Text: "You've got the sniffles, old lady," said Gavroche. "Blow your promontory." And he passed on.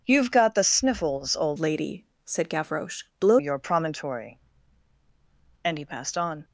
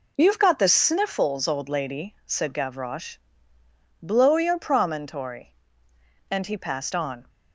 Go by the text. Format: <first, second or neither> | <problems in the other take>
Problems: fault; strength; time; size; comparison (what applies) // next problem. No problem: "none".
second | changes voice from "lady" to "Blow"; from 1.5 to 3.3 s; 1.8 s long